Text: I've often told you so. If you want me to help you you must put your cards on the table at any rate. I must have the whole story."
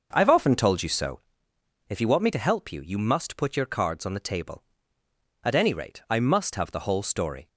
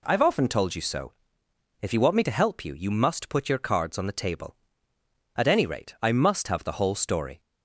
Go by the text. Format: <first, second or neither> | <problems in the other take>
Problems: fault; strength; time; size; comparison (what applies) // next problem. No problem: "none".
second | starts louder than the rest; noticeable; until 1.3 s; 6 dB